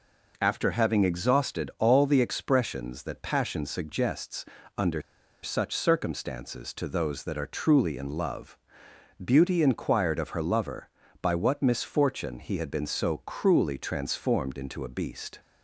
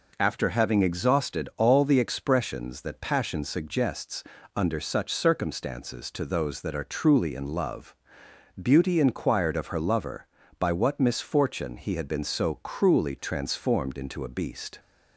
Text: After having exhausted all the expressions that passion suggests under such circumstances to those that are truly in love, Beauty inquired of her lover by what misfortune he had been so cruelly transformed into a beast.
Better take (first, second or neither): second